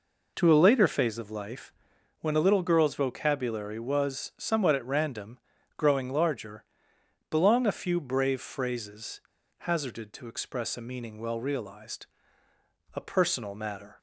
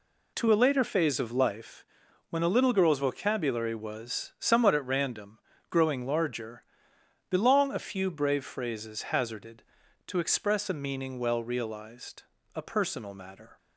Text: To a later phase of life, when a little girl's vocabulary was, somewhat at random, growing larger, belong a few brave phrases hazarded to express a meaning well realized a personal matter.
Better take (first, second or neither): second